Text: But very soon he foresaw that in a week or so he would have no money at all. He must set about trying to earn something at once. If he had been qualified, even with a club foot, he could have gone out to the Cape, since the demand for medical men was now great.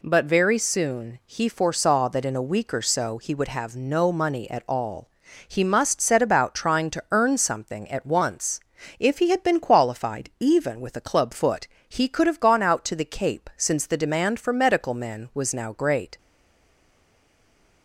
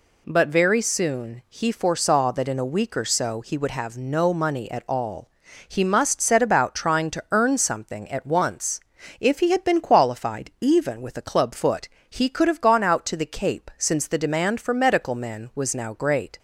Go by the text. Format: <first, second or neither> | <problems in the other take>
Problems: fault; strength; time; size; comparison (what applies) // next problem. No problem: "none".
second | stays silent after the last word; noticeable; from 16.1 s on; 1.7 s long